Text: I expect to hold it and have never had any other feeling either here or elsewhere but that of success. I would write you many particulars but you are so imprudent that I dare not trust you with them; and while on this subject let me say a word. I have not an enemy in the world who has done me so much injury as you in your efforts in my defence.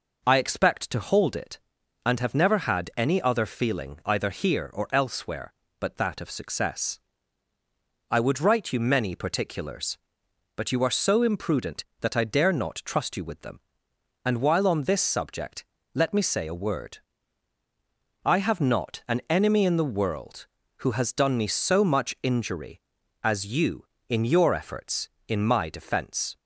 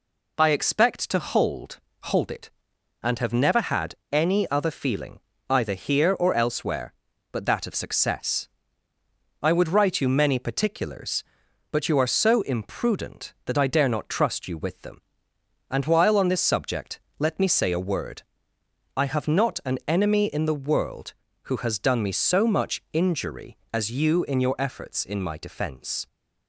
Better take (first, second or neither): first